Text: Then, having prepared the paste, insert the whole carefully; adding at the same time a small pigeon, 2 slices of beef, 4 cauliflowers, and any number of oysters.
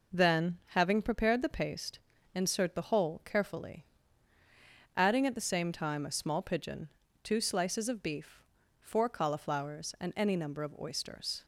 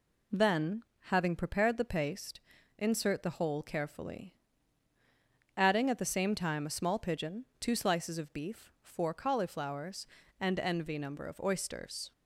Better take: first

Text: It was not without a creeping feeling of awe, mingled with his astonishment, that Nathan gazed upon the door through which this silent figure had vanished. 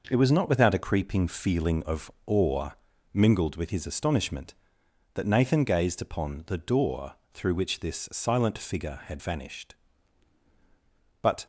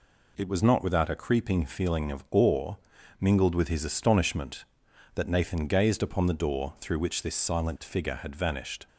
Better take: second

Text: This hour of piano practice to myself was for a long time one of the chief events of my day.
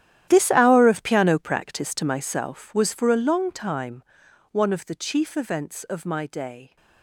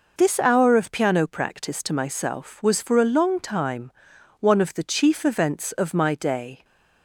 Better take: second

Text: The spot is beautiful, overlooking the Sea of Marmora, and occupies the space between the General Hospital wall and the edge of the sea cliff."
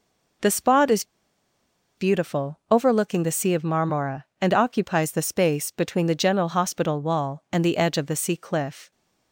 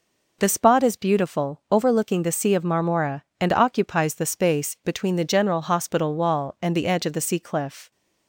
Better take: second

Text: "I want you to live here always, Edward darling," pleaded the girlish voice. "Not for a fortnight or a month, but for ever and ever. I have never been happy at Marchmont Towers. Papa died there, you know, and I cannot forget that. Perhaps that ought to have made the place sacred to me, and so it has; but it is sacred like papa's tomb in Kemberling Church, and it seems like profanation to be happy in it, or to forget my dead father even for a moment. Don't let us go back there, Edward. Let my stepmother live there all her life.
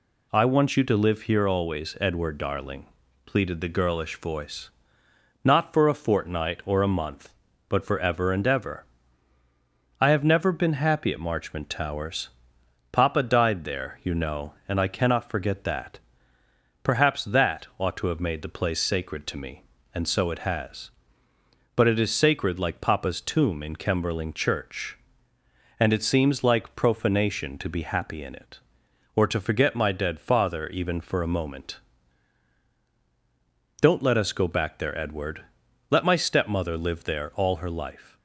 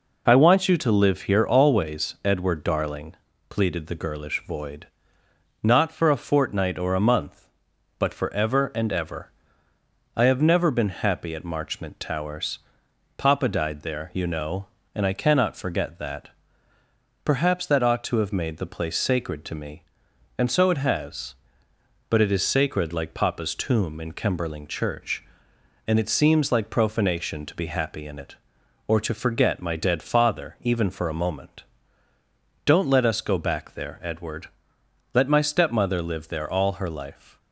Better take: first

